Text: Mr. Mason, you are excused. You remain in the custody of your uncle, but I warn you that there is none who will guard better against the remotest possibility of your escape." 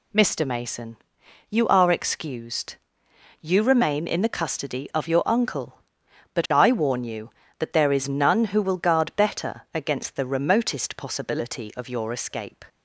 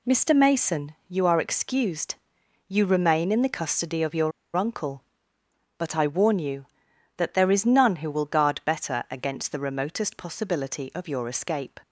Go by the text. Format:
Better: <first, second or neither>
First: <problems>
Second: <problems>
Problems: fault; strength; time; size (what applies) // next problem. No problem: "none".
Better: first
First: none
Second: pauses between "your" and "uncle"; slight; at 4.3 s; 0.25 s long